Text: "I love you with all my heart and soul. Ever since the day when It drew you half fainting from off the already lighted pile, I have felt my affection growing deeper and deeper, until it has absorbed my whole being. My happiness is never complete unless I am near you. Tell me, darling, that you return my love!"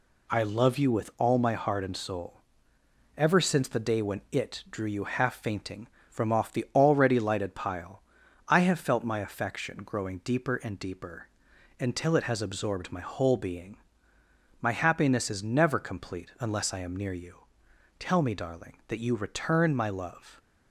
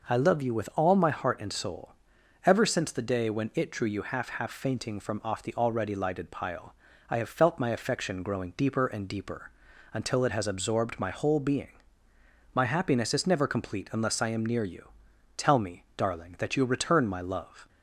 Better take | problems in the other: first | says "half" twice; at 4.3 s

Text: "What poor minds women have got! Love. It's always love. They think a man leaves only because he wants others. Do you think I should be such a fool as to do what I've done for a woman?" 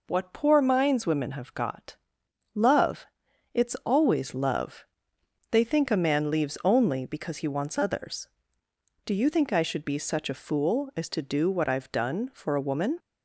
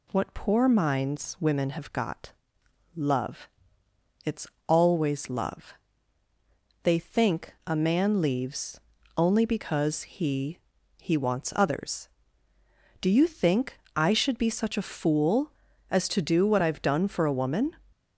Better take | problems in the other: first | pauses between "It's" and "always"; slight; at 4.4 s; 0.20 s long // pauses between "leaves" and "only"; at 8.8 s; 0.38 s long // says "he" twice; at 10.9 s // pauses between "think" and "I"; slight; at 13.7 s; 0.16 s long

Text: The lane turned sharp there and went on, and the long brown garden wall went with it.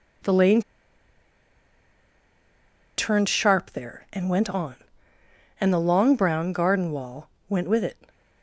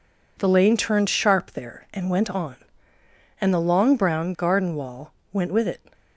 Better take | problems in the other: second | pauses between "lane" and "turned"; strong; at 0.6 s; 2.3 s long // pauses between "wall" and "went"; slight; at 7.2 s; 0.18 s long; slight in the second

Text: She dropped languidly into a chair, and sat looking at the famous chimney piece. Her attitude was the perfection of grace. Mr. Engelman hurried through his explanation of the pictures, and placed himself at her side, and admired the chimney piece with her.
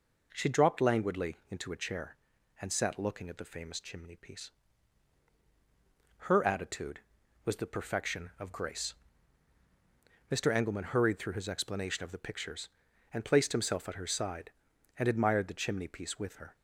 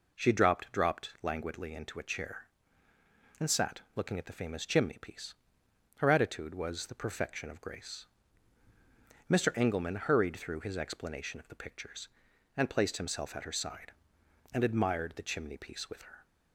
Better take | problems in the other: first | says "dropped" twice; at 0.7 s // pauses between "sat" and "looking"; slight; at 3.7 s; 0.16 s long

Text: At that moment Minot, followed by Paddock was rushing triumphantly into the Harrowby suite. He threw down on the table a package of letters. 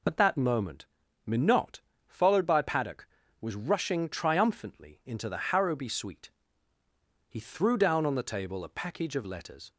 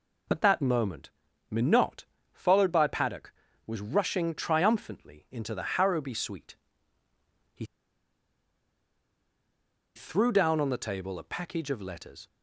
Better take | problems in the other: first | pauses between "moment" and "Minot"; at 1.0 s; 0.40 s long; also in the first // pauses between "He" and "threw"; strong; at 7.6 s; 2.3 s long

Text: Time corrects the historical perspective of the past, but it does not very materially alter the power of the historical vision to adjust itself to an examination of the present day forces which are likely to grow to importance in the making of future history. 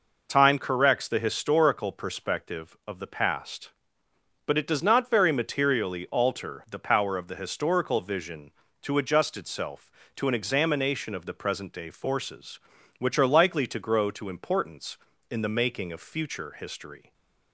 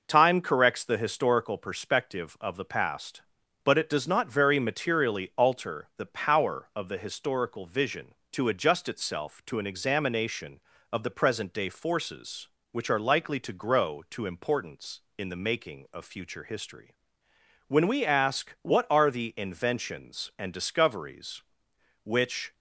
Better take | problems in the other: first | goes on to say "When we ask what are the inventions and discoveries which"; strong; from 17.6 s on; 4.8 s long

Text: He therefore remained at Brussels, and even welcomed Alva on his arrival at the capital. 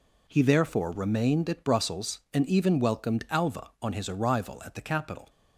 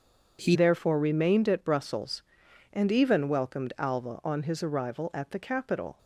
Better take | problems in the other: first | starts louder than the rest; until 1.4 s; 7 dB // changes voice at "therefore"; from 0.5 s on; 5.4 s long

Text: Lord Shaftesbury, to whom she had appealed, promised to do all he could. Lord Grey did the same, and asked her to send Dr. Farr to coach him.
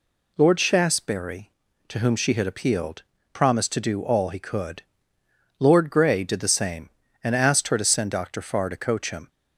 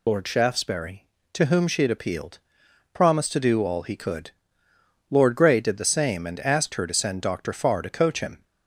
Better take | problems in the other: first | loses the start of "Lord"; at 0.0 s; 50 ms

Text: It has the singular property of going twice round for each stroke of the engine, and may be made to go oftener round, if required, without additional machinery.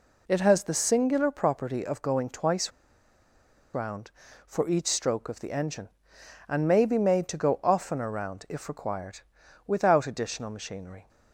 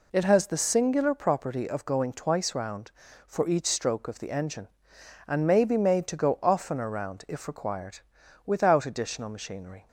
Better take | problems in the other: second | pauses between "twice" and "round"; at 2.7 s; 1.0 s long

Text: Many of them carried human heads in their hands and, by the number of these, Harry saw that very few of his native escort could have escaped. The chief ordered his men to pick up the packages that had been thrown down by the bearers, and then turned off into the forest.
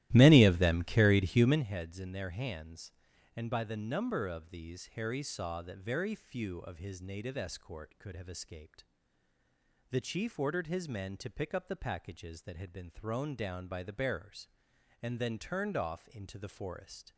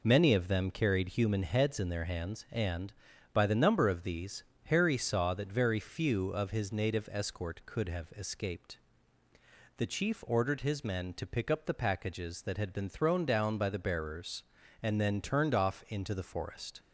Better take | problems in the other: second | starts louder than the rest; strong; until 1.7 s; 15.5 dB

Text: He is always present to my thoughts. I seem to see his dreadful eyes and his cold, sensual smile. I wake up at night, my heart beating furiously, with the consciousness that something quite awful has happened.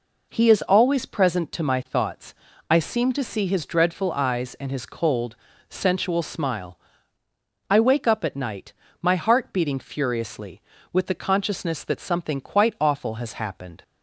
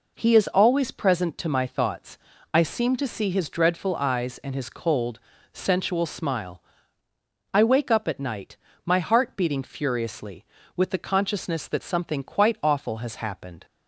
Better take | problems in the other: neither | none

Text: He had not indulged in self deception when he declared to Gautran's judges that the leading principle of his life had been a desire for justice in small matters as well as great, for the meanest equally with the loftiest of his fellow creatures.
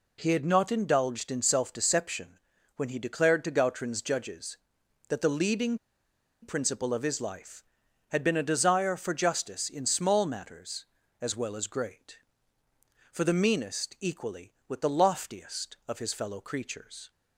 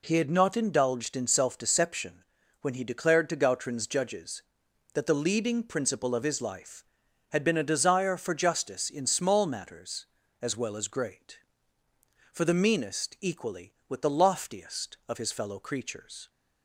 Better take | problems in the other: second | pauses between "deception" and "when"; slight; at 2.3 s; 0.36 s long; slight in the second // pauses between "leading" and "principle"; noticeable; at 5.7 s; 0.64 s long

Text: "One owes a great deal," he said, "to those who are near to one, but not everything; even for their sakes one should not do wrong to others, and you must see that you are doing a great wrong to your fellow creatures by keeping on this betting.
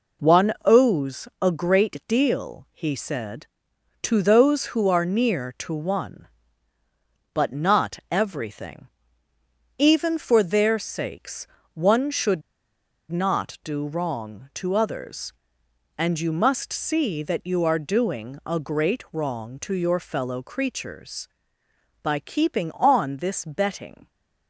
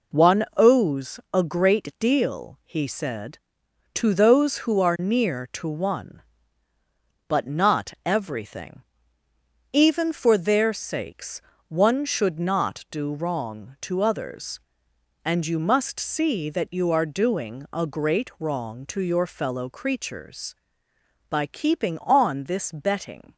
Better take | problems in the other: second | pauses between "sakes" and "one"; slight; at 11.4 s; 0.26 s long; slight in the second // pauses between "should" and "not"; noticeable; at 12.4 s; 0.70 s long

